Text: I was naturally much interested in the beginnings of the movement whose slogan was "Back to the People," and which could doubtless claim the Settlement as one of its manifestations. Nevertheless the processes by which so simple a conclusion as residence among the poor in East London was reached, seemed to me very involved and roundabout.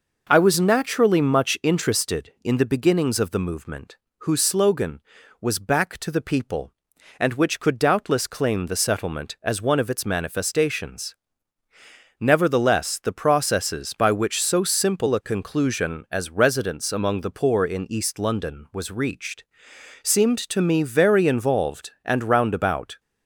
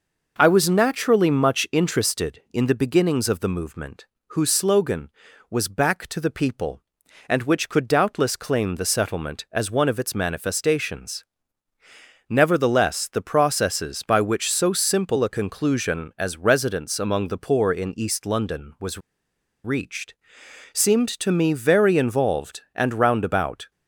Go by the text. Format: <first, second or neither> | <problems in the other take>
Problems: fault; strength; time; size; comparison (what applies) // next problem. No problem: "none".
first | pauses between "movement" and "whose"; slight; at 4.0 s; 0.24 s long; slight in the first // pauses between "was" and "reached"; noticeable; at 18.9 s; 0.65 s long